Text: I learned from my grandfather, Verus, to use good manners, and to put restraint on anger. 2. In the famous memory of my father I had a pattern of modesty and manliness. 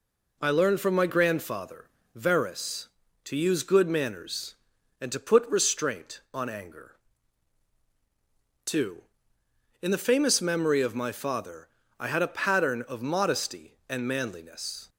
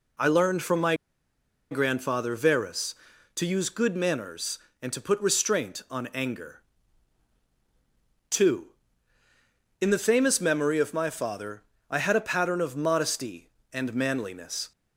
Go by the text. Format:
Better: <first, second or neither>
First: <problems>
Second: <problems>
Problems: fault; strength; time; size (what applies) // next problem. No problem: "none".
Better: first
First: pauses between "father" and "I"; slight; at 11.6 s; 0.32 s long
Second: pauses between "my" and "grandfather"; noticeable; at 0.9 s; 0.76 s long // pauses between "father" and "I"; slight; at 11.6 s; 0.28 s long